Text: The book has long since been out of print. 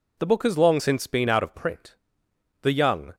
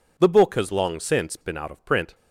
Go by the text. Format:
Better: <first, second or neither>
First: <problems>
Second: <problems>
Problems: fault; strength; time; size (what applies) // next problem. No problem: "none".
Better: second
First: goes on to say "The young"; from 2.6 s on; 0.54 s long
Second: none